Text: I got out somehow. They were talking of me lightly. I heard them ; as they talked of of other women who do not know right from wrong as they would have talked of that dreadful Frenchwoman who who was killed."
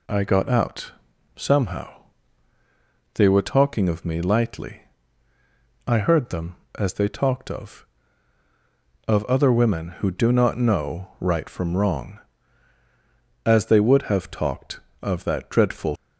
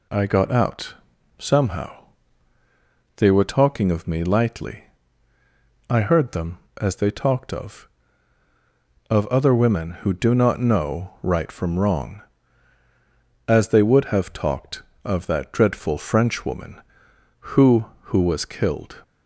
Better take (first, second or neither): second